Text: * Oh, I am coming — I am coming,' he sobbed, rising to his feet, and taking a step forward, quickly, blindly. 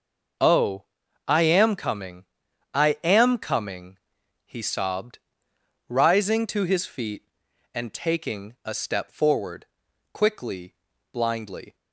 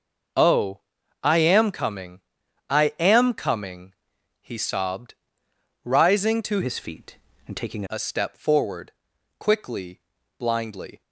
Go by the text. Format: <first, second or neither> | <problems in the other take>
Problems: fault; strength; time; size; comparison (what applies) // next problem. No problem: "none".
first | changes voice from "his" to "taking"; from 6.6 to 7.8 s; 1.2 s long